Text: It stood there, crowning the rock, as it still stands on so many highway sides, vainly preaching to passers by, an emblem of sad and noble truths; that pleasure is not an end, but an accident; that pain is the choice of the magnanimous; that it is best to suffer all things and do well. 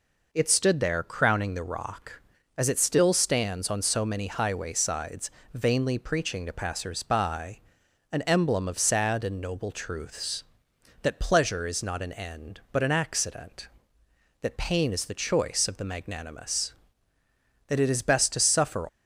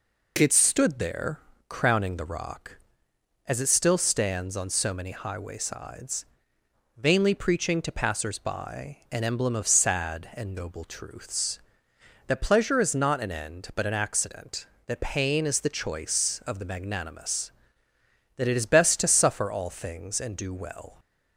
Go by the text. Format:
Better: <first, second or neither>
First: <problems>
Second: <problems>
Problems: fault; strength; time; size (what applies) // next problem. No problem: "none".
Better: second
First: stops before "all things and do well"; at 18.8 s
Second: none